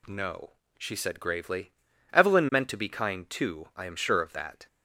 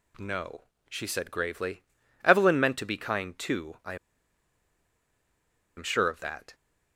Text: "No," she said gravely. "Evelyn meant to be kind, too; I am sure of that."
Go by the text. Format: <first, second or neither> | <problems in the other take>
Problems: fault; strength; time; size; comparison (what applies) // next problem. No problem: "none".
first | pauses between "I" and "am"; strong; at 3.9 s; 1.8 s long